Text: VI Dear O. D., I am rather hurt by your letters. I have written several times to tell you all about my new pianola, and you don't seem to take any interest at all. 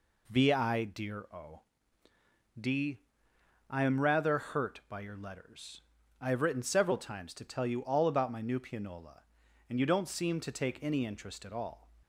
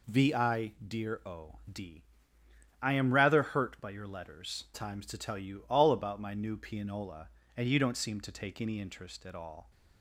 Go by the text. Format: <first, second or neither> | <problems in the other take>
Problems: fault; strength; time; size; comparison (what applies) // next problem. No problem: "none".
first | skips "I have written several"; at 4.6 s